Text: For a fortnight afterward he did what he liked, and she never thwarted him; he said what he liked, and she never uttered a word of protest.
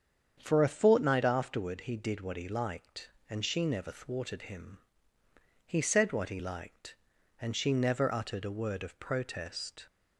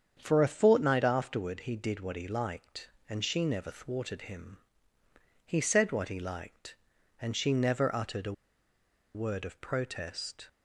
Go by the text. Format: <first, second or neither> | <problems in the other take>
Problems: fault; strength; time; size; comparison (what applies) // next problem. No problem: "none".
first | starts louder than the rest; strong; until 1.2 s; 7.5 dB; strong in the first // pauses between "a" and "word"; noticeable; at 8.3 s; 0.82 s long